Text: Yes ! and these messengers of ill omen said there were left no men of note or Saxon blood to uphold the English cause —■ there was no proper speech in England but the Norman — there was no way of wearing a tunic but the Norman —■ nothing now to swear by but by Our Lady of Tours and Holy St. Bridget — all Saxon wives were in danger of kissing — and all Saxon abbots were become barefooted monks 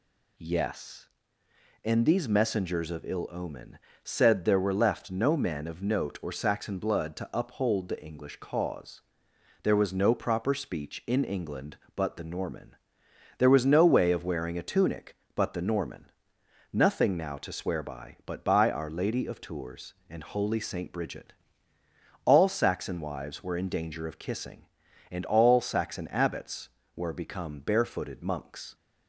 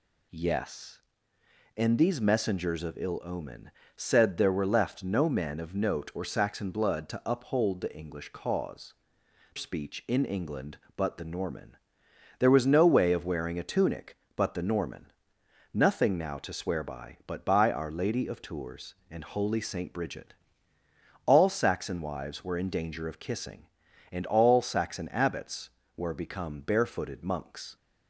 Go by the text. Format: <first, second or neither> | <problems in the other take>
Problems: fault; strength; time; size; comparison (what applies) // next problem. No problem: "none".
first | pauses between "omen" and "said"; slight; at 3.7 s; 0.24 s long; slight in the first // skips "there was no proper"; at 9.2 s